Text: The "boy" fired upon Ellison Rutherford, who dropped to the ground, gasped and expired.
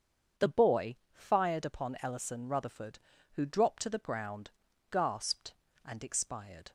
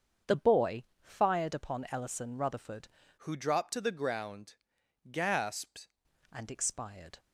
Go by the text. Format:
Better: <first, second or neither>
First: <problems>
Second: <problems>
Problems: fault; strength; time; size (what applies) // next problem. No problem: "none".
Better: first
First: starts louder than the rest; strong; until 1.5 s; 7 dB // pauses between "boy" and "fired"; slight; at 0.9 s; 0.16 s long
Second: starts louder than the rest; until 1.4 s; 7 dB // pauses between "boy" and "fired"; slight; at 0.8 s; 0.18 s long // changes voice from "who" to "gasped"; from 3.1 to 5.8 s; 2.7 s long